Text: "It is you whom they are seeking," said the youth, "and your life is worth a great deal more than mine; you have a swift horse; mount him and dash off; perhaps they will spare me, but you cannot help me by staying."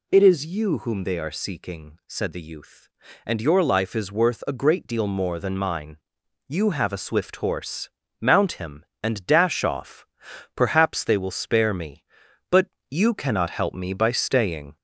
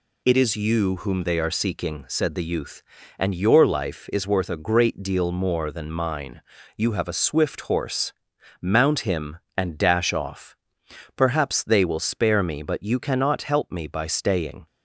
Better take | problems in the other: second | gets louder; slight; throughout; 2 dB // pauses between "but" and "you"; slight; at 12.6 s; 0.22 s long

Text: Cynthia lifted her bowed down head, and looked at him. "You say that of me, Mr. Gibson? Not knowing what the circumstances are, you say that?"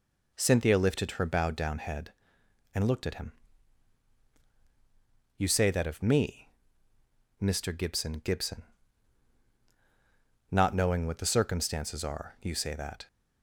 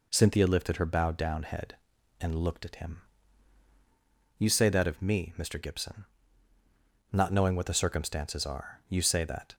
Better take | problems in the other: second | says "Gibson" twice; at 8.1 s

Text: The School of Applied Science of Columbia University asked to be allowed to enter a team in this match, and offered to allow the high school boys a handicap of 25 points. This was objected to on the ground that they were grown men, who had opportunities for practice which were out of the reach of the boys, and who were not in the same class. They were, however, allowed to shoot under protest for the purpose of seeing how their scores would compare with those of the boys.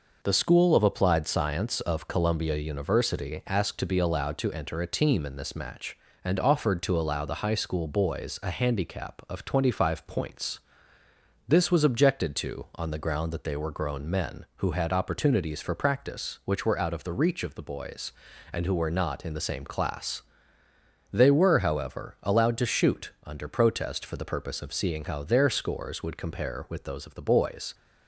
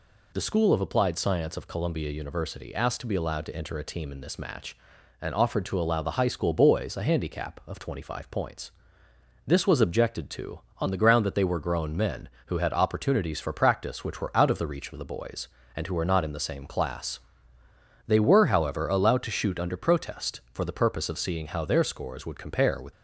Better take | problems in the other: first | stops before "those of the boys"; at 22.9 s

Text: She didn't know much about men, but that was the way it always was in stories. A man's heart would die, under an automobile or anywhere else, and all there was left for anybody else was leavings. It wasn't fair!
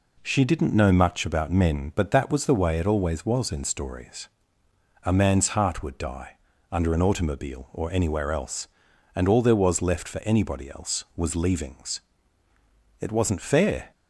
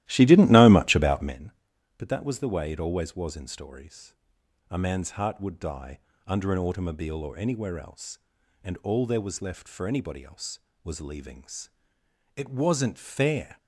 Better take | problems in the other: first | starts louder than the rest; strong; until 1.4 s; 15 dB

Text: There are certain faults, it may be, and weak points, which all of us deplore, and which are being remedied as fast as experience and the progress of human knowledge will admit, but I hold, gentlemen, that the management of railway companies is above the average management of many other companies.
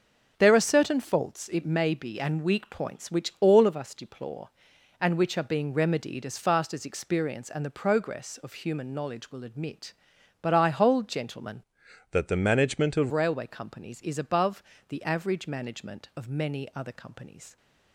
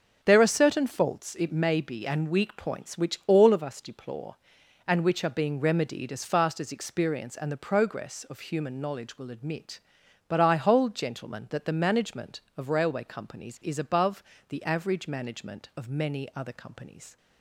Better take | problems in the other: second | starts louder than the rest; noticeable; until 1.3 s; 6 dB; noticeable in the second // changes voice from "that" to "of"; from 12.1 to 13.1 s; 1.0 s long // pauses between "above" and "the"; slight; at 14.6 s; 0.26 s long; slight in the second

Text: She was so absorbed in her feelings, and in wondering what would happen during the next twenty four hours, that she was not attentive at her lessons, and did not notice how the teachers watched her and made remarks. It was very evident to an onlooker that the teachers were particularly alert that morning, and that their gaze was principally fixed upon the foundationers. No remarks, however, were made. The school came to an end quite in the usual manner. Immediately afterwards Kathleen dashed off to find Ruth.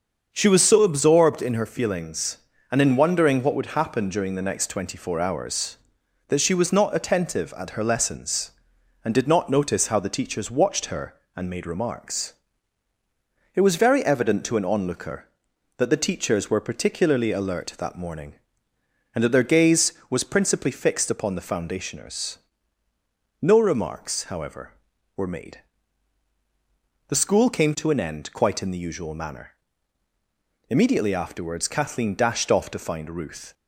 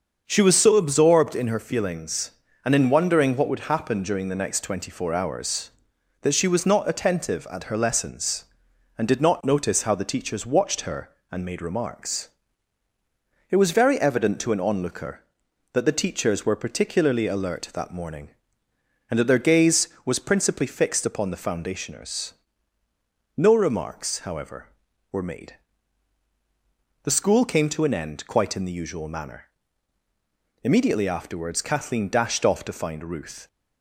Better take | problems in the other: neither | starts louder than the rest; the same in both

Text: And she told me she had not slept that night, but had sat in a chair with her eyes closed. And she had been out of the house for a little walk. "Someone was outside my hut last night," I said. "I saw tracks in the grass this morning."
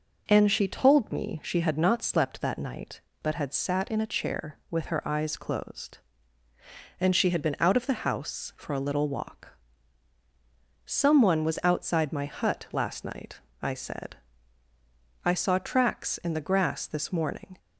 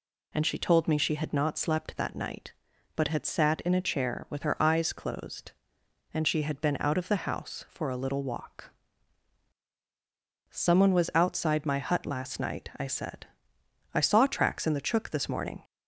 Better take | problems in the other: first | says "chook" for "grass"; at 14.7 s

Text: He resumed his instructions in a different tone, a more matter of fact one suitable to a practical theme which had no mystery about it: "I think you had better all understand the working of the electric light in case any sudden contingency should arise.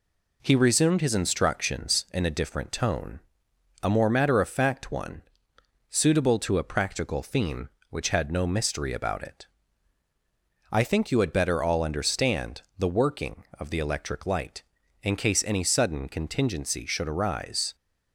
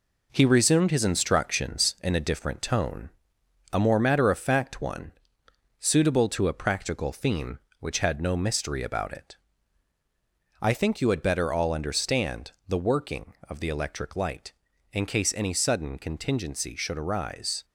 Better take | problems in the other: first | gets quieter; noticeable; throughout; 5.5 dB // pauses between "one" and "suitable"; noticeable; at 5.1 s; 0.70 s long; noticeable in the first

